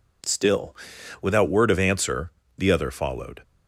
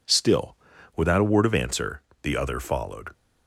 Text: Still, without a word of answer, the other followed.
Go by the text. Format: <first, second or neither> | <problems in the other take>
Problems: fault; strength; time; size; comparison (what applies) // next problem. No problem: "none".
second | skips "a"; at 1.4 s